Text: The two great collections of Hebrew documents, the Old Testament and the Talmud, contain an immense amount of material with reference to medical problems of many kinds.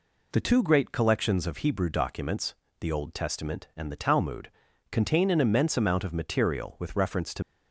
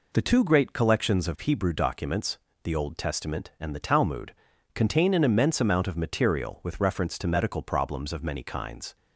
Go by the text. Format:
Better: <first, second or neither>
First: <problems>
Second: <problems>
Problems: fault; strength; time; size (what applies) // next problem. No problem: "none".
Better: second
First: stops before "medical problems of many kinds"; at 7.4 s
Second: none